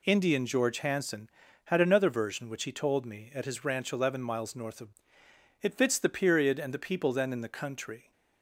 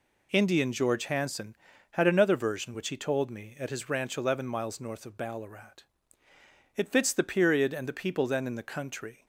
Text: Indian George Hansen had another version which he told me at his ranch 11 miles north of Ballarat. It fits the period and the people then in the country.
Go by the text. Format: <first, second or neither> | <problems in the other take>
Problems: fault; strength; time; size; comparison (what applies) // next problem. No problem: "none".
second | skips "Ballarat"; at 5.2 s